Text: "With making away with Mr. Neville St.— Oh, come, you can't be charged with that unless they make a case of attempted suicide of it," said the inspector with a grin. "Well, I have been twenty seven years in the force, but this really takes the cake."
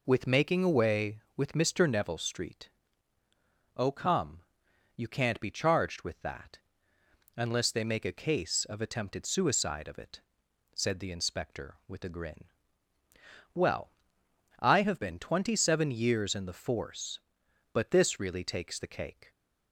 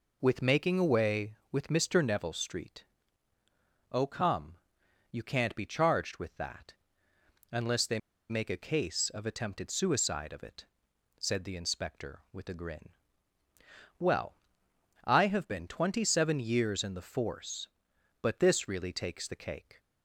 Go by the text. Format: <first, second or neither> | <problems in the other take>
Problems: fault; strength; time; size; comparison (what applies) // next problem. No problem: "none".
first | pauses between "that" and "unless"; noticeable; at 6.7 s; 0.76 s long; noticeable in the first // pauses between "they" and "make"; slight; at 7.9 s; 0.32 s long